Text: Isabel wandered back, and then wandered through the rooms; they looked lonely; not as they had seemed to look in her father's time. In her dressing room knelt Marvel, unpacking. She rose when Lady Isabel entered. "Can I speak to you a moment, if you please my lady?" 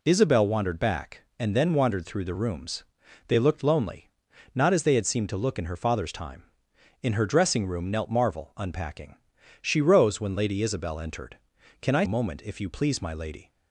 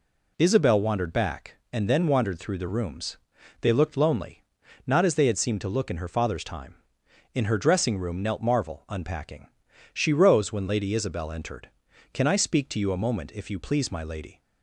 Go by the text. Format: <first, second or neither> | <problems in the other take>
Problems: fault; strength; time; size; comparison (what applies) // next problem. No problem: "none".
second | skips "speak to you"; at 12.0 s